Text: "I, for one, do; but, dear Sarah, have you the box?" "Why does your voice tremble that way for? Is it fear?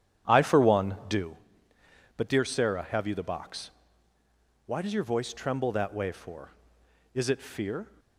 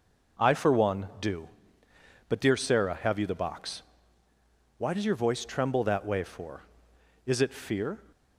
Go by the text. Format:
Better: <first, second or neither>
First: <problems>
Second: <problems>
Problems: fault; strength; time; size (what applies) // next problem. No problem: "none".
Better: second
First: starts louder than the rest; strong; until 1.4 s; 9.5 dB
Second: none